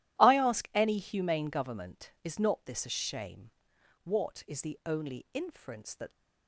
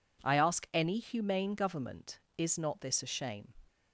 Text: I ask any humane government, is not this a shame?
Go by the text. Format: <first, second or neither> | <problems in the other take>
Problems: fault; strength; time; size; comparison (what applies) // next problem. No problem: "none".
second | goes on to say "What is the only inference that"; strong; from 4.0 s on; 2.0 s long